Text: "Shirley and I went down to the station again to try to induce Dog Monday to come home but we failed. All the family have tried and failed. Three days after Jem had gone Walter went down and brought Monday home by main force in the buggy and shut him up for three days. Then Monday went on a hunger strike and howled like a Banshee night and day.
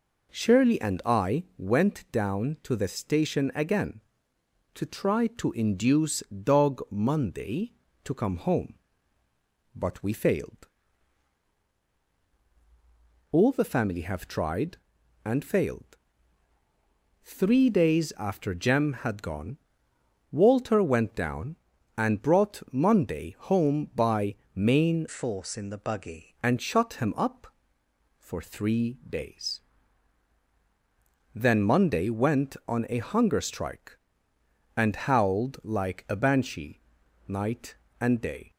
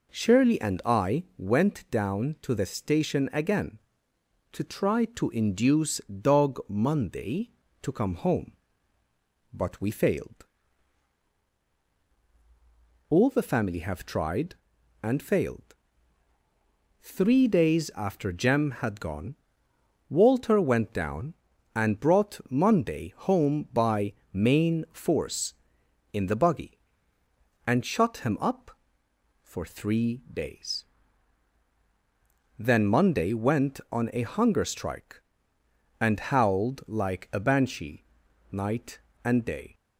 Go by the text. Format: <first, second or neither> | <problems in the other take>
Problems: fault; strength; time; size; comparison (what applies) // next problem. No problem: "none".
second | pauses between "gone" and "Walter"; noticeable; at 19.5 s; 0.74 s long; noticeable in the second // pauses between "by" and "main"; slight; at 24.3 s; 0.18 s long; slight in the second // changes voice from "force" to "buggy"; from 25.0 to 26.3 s; 1.3 s long // pauses between "Banshee" and "night"; noticeable; at 36.8 s; 0.46 s long; noticeable in the second